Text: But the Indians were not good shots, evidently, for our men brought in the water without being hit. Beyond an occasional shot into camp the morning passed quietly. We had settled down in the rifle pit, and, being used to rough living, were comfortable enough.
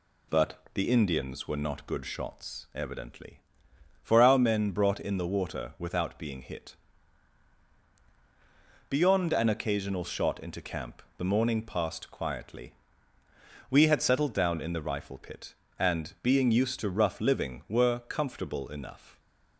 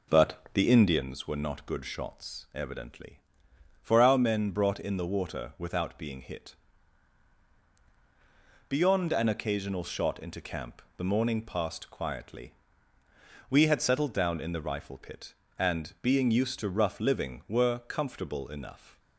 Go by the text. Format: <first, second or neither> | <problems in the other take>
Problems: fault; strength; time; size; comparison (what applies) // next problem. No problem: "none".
first | starts louder than the rest; until 1.1 s; 3.5 dB // pauses between "camp" and "the"; slight; at 10.8 s; 0.16 s long; slight in the first